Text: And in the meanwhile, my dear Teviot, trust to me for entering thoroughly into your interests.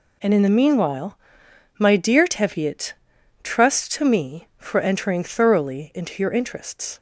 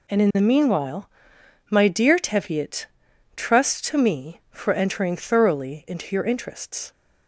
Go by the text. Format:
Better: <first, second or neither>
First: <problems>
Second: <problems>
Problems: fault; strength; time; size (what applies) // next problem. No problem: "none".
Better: neither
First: none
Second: none